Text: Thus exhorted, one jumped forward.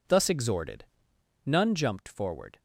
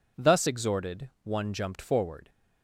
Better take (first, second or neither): second